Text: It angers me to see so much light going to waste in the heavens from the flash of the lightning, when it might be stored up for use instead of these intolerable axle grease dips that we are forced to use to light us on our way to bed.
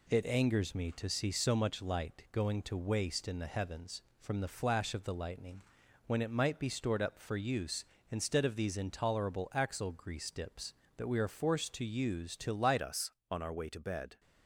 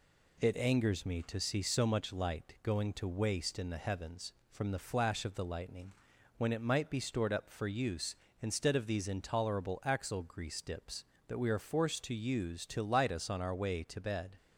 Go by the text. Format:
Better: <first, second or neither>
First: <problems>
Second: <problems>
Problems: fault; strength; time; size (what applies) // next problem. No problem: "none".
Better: second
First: changes voice at "us"; from 12.7 s on; 1.4 s long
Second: none